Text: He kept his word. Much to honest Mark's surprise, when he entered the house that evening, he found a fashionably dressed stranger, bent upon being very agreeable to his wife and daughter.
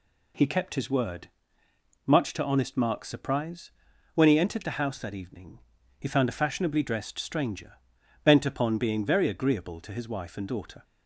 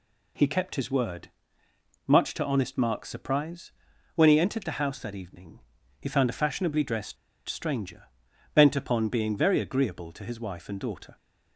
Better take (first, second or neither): first